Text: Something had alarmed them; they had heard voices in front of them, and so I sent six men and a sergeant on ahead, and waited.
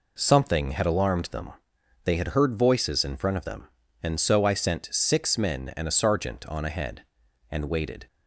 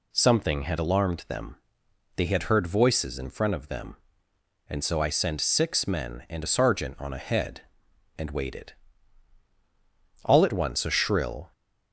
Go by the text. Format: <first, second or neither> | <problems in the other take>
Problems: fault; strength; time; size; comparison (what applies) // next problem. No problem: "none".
first | goes on to say "All at once a shrill"; noticeable; from 10.2 s on; 1.2 s long